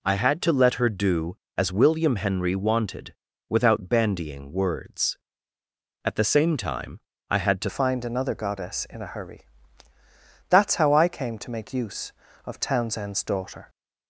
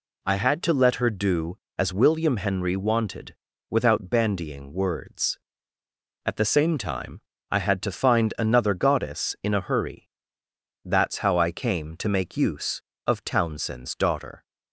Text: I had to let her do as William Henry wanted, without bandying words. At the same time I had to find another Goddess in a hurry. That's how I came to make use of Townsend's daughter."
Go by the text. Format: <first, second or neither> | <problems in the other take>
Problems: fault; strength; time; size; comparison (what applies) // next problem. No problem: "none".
second | pauses between "time" and "I"; slight; at 7.0 s; 0.28 s long; slight in the second // changes voice at "find"; from 7.6 s on; 6.0 s long